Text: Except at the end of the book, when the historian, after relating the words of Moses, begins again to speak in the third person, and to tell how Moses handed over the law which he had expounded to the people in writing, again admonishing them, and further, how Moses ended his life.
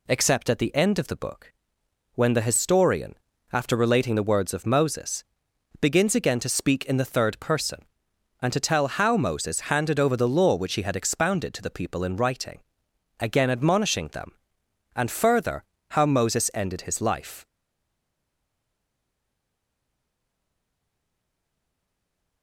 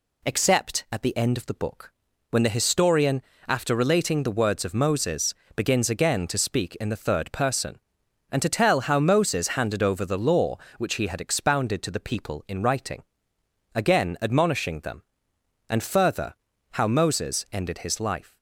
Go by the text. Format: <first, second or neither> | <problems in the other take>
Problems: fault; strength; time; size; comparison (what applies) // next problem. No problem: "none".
second | stays silent after the last word; strong; from 17.4 s on; 5.0 s long